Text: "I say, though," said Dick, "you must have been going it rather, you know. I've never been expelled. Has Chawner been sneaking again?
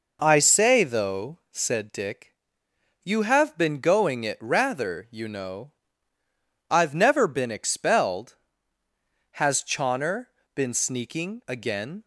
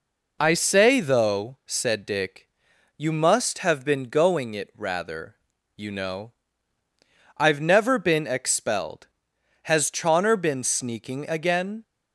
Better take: second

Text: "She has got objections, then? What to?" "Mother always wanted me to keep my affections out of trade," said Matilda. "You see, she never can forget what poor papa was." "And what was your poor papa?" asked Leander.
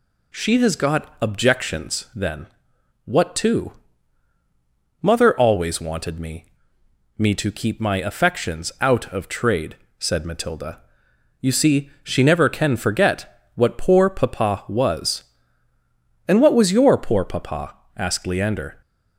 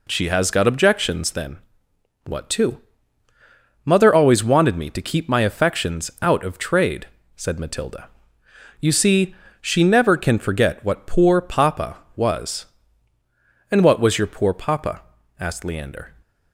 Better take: second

